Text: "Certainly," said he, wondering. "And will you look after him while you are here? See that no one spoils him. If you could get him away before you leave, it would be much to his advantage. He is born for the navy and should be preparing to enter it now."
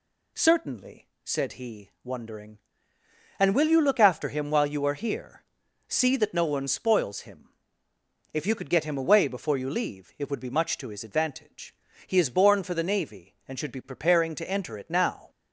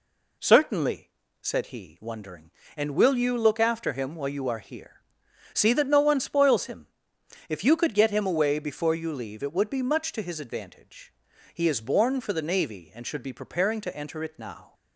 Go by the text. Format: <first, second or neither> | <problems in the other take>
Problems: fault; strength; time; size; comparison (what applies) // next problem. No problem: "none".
neither | none